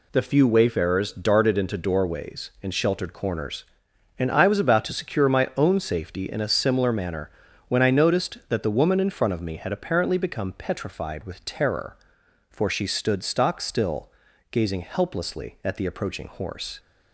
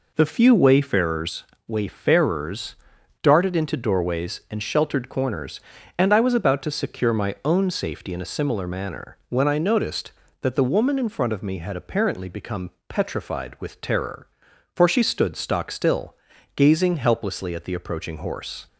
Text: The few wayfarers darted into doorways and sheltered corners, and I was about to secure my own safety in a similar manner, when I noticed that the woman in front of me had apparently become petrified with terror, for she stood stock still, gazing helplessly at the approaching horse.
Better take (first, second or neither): first